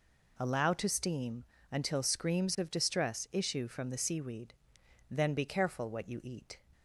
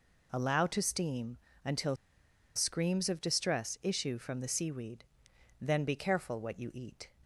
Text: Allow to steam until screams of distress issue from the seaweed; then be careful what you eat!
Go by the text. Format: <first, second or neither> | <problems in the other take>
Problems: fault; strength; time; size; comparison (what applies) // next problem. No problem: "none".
first | pauses between "steam" and "until"; slight; at 1.3 s; 0.26 s long; slight in the first // pauses between "until" and "screams"; noticeable; at 1.9 s; 0.60 s long